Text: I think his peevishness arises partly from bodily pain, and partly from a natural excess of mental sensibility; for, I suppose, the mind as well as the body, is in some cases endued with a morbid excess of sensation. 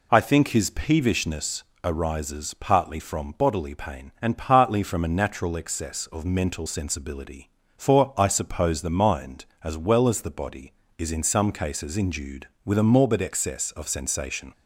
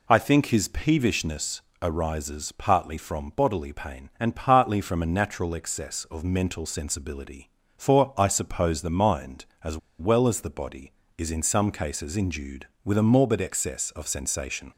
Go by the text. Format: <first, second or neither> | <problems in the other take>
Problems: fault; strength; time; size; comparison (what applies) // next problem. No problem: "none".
first | pauses between "peevishness" and "arises"; slight; at 1.6 s; 0.20 s long; slight in the first // pauses between "as" and "well"; slight; at 9.7 s; 0.21 s long